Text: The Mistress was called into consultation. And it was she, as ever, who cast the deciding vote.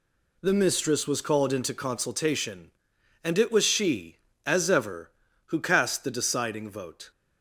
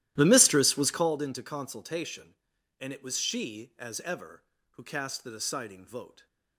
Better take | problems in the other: first | starts louder than the rest; strong; until 1.1 s; 14 dB

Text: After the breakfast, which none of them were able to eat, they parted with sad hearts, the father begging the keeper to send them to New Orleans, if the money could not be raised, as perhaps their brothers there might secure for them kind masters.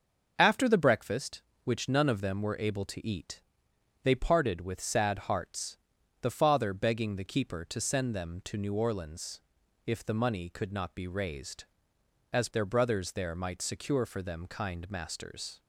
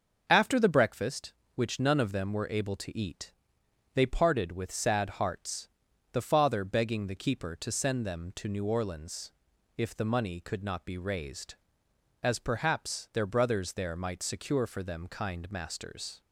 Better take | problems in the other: second | starts louder than the rest; until 1.3 s; 6.5 dB; also in the second // skips "perhaps"; at 12.4 s

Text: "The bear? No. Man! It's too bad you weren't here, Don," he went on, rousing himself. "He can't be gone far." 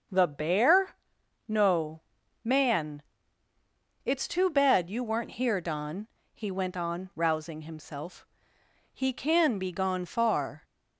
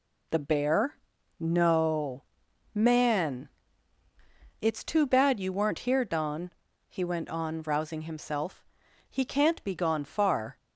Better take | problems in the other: second | says "can" for "can't"; at 9.1 s

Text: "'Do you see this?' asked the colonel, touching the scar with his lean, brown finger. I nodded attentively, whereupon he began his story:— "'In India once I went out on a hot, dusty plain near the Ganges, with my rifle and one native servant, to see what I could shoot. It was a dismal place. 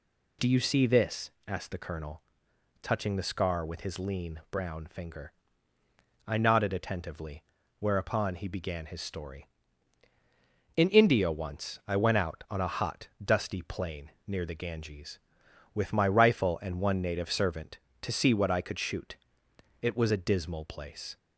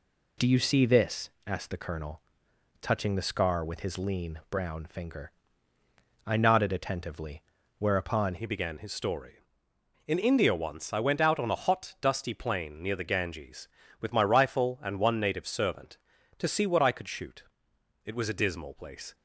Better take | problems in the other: first | changes voice at "he"; from 8.3 s on; 10.8 s long

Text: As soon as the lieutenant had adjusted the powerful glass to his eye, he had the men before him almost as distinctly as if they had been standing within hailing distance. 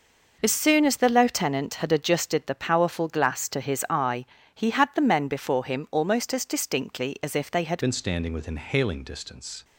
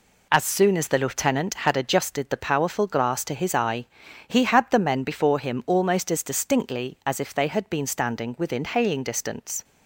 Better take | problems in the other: second | changes voice at "been"; from 7.8 s on; 1.8 s long

